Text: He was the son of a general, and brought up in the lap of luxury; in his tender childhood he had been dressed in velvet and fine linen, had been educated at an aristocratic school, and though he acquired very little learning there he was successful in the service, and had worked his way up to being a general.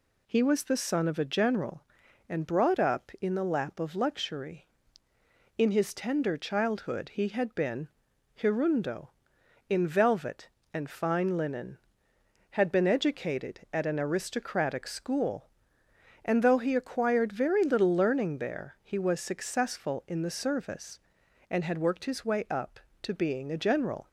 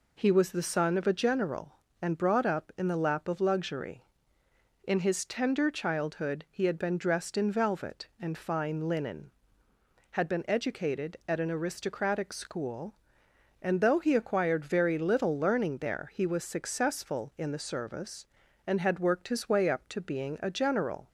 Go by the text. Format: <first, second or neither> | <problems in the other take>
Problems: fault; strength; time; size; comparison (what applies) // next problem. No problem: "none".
second | says "hirundo" for "dressed"; at 8.3 s